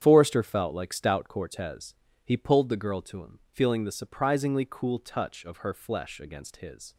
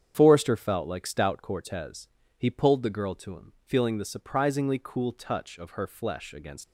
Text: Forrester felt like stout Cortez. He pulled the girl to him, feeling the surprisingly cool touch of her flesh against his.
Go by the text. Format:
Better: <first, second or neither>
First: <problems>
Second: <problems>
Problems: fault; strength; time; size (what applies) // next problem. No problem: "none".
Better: first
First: starts louder than the rest; strong; until 1.0 s; 8.5 dB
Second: starts louder than the rest; strong; until 1.1 s; 8 dB // stops before "his"; at 6.6 s